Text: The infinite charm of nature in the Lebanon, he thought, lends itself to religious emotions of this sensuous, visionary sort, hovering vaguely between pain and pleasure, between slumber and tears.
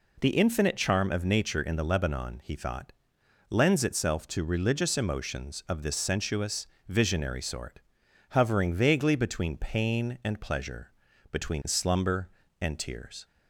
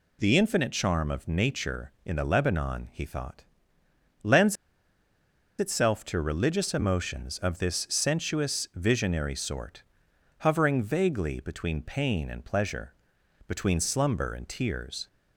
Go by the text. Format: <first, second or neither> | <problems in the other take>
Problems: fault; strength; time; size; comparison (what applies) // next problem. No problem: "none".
first | pauses between "lends" and "itself"; at 4.5 s; 1.0 s long